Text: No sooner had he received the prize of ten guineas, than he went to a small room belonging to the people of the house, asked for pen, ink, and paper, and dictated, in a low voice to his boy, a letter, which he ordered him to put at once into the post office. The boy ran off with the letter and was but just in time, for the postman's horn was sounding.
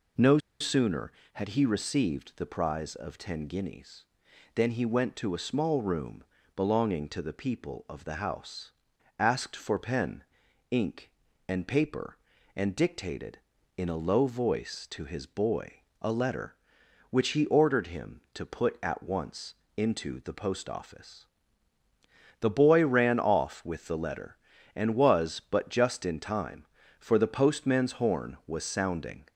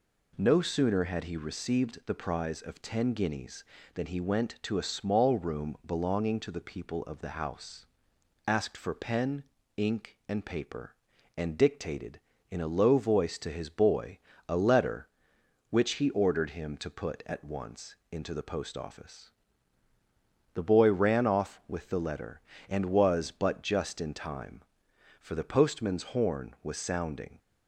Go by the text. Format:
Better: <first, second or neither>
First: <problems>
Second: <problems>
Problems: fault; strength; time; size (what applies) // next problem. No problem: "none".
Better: second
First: pauses between "No" and "sooner"; slight; at 0.3 s; 0.22 s long // pauses between "room" and "belonging"; slight; at 6.2 s; 0.32 s long // pauses between "once" and "into"; slight; at 19.5 s; 0.24 s long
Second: pauses between "once" and "into"; slight; at 17.9 s; 0.16 s long